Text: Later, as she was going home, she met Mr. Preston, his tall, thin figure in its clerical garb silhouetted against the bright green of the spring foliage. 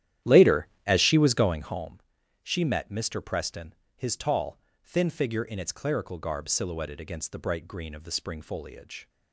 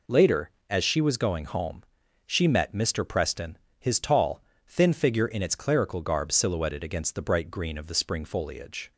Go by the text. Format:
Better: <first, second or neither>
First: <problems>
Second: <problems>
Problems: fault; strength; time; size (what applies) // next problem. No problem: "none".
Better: second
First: starts louder than the rest; strong; until 1.8 s; 11.5 dB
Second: none